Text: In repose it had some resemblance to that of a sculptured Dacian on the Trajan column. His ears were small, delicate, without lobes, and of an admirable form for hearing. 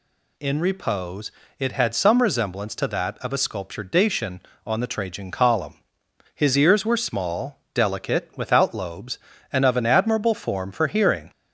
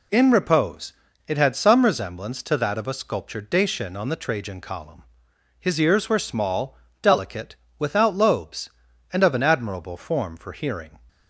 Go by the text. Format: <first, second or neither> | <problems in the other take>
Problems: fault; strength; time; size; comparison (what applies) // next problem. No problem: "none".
neither | pauses between "repose" and "it"; slight; the same in both